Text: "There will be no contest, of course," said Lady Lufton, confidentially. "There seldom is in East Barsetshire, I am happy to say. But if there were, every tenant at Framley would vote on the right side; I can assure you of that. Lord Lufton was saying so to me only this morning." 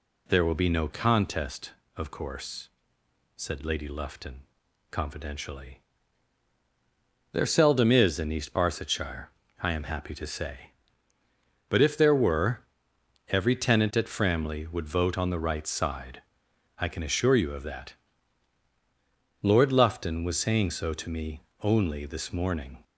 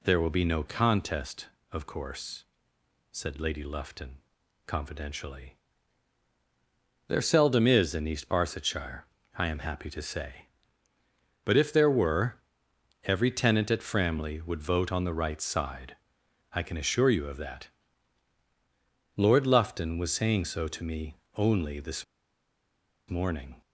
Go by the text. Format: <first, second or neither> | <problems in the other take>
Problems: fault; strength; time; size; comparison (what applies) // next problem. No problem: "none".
first | pauses between "me" and "only"; slight; at 21.1 s; 0.22 s long; slight in the first // pauses between "this" and "morning"; at 22.0 s; 1.0 s long